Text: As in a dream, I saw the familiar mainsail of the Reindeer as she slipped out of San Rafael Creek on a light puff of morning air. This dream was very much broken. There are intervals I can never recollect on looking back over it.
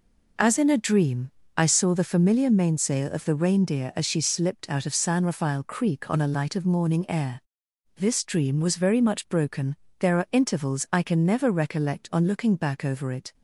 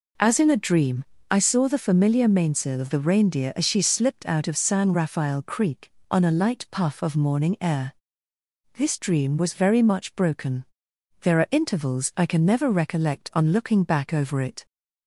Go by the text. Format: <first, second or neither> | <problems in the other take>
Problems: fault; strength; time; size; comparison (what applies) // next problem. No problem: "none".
second | skips "puff"; at 6.5 s